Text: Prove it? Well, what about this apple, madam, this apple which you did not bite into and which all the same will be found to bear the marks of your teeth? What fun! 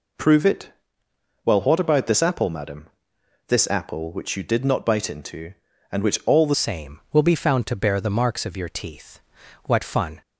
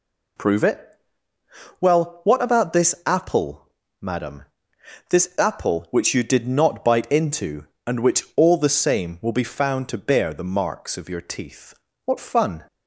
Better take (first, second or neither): second